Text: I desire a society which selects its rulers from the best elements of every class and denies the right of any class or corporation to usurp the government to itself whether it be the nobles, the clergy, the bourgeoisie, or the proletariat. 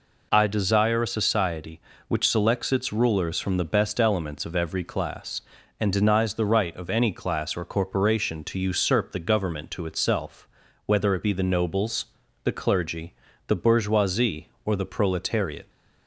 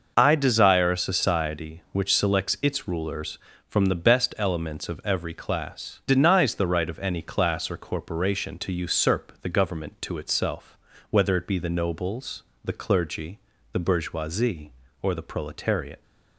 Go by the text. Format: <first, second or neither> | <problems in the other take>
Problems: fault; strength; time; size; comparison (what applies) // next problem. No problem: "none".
first | skips "and"; at 6.0 s // pauses between "itself" and "whether"; slight; at 10.7 s; 0.32 s long; slight in the first